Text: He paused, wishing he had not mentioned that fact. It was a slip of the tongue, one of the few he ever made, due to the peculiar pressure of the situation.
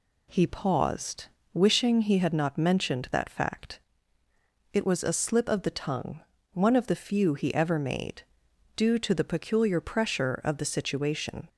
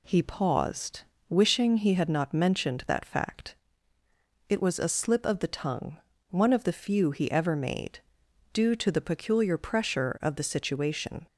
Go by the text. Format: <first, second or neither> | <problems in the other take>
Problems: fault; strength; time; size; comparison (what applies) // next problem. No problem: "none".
neither | none